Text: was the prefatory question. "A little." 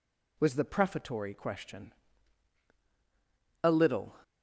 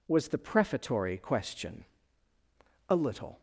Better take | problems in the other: neither | none

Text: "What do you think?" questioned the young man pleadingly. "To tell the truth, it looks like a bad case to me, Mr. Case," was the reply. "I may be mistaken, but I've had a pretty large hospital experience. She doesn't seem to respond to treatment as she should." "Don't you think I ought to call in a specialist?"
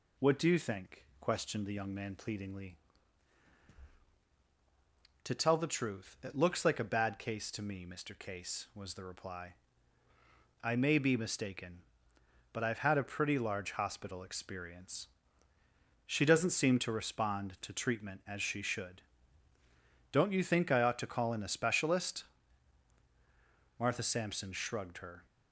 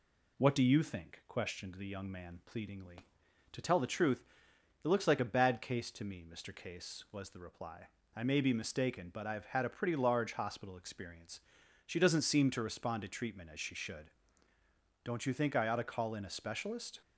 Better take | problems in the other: second | goes on to say "Martha Sampson shrugged her"; from 23.7 s on; 1.4 s long

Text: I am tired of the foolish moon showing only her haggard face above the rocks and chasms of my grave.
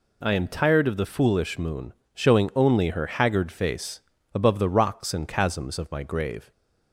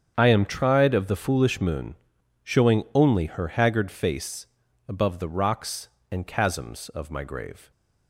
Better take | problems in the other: first | starts louder than the rest; strong; until 1.1 s; 7.5 dB // says "tried" for "tired"; at 0.4 s // pauses between "moon" and "showing"; noticeable; at 1.9 s; 0.48 s long; slight in the first // pauses between "face" and "above"; at 4.4 s; 0.42 s long; slight in the first

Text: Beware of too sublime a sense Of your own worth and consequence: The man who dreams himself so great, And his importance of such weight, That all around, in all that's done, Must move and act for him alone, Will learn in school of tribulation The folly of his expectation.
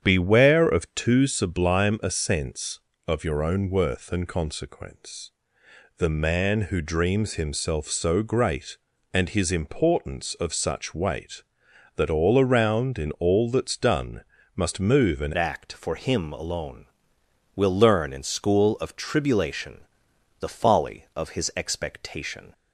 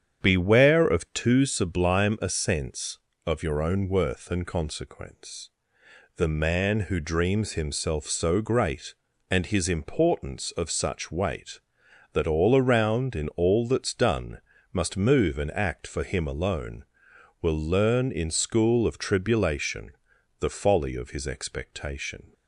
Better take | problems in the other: second | starts louder than the rest; strong; until 1.0 s; 8.5 dB; strong in the second // changes voice at "act"; from 15.3 s on; 7.2 s long // pauses between "tribulation" and "The"; noticeable; at 19.8 s; 0.56 s long; noticeable in the second

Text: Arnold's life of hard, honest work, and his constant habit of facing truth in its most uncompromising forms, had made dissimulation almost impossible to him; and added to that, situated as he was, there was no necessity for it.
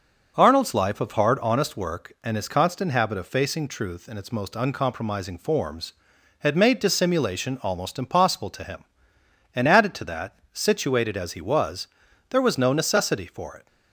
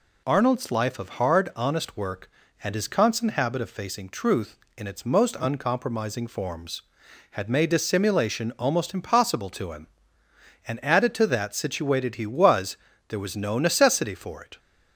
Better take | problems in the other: first | skips "as"; at 12.1 s

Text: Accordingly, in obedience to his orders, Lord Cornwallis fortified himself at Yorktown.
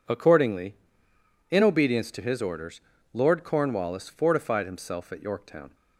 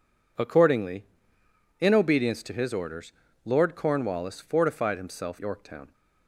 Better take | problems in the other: first | skips "at"; at 5.3 s

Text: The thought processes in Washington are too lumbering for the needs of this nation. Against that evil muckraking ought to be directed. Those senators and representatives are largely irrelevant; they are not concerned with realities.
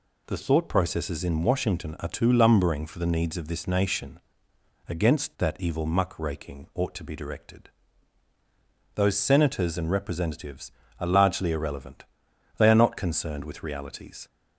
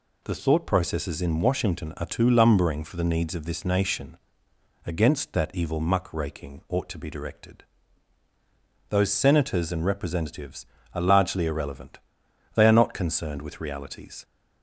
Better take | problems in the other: neither | none

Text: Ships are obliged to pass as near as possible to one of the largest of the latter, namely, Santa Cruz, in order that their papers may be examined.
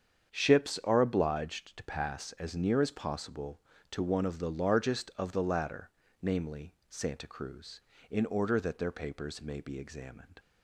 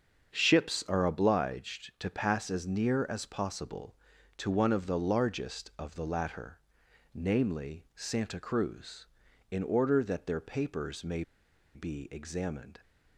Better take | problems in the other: first | starts louder than the rest; strong; until 1.4 s; 7 dB; strong in the first // pauses between "may" and "be"; noticeable; at 11.2 s; 0.52 s long

